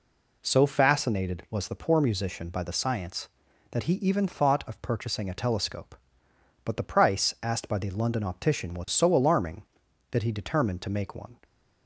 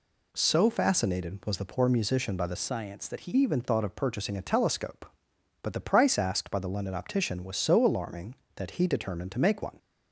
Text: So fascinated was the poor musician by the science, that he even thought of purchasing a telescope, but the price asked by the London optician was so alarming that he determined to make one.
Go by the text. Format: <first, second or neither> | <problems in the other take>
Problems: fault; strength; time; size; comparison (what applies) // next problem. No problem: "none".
first | changes voice from "science" to "he"; from 2.5 to 3.3 s; 0.8 s long